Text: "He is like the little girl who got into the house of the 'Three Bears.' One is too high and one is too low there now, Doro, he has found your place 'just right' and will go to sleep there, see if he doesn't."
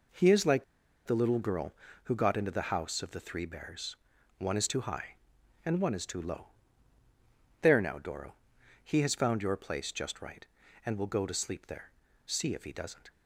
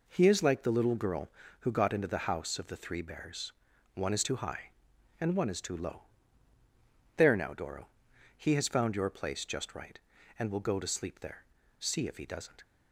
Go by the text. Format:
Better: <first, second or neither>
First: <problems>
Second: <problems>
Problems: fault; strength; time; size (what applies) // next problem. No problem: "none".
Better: second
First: pauses between "like" and "the"; at 0.6 s; 0.40 s long // pauses between "low" and "there"; at 6.4 s; 1.1 s long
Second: pauses between "low" and "there"; at 6.0 s; 1.1 s long